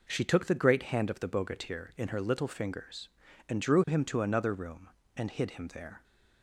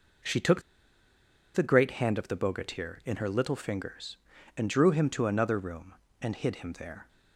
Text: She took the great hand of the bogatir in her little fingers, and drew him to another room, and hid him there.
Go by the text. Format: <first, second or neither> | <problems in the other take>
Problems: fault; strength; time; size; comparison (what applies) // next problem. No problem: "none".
first | pauses between "took" and "the"; noticeable; at 0.6 s; 0.92 s long